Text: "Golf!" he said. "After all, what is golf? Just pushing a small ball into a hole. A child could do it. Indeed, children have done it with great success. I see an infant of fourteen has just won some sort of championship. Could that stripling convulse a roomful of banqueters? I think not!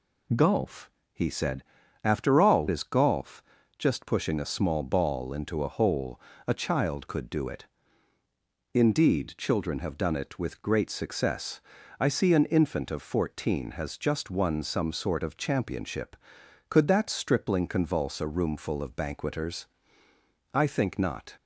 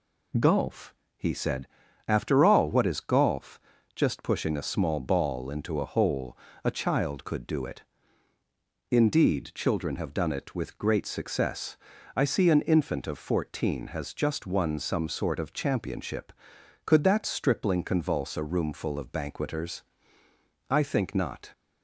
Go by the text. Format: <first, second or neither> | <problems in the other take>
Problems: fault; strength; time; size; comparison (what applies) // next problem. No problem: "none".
second | skips "what"; at 2.6 s